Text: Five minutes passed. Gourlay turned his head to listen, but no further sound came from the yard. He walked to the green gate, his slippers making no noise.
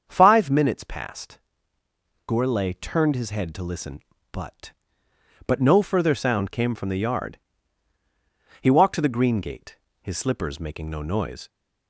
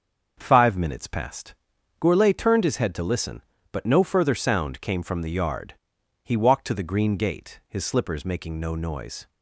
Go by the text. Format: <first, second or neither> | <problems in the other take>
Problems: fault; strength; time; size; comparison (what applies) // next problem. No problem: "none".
second | starts louder than the rest; strong; until 1.0 s; 7 dB; also in the second // says "but" twice; at 5.4 s